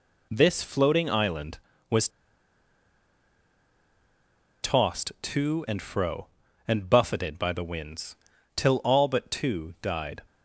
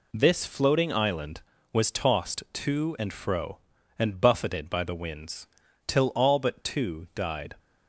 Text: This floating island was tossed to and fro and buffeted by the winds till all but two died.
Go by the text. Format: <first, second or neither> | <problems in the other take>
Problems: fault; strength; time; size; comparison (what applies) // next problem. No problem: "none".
second | pauses between "was" and "tossed"; strong; at 2.0 s; 2.5 s long // pauses between "winds" and "till"; at 8.1 s; 0.38 s long; also in the second